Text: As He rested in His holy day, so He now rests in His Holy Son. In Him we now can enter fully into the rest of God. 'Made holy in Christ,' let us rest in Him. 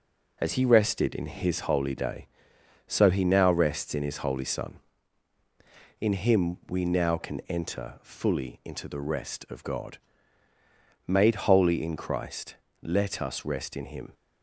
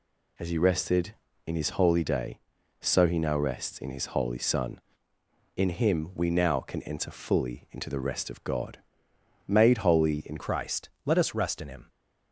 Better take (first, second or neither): first